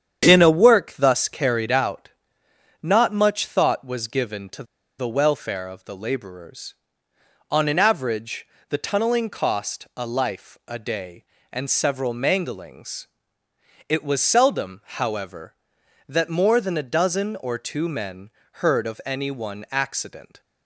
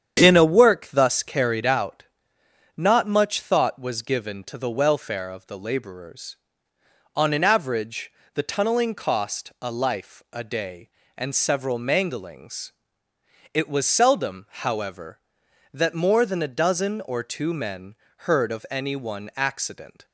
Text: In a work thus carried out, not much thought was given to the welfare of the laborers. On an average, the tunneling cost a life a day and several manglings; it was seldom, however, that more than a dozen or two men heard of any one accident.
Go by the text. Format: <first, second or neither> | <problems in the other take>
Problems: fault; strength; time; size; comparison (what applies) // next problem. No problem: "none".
second | starts louder than the rest; strong; until 1.3 s; 8.5 dB; strong in the second // pauses between "to" and "the"; slight; at 4.6 s; 0.34 s long // pauses between "men" and "heard"; slight; at 18.3 s; 0.34 s long; slight in the second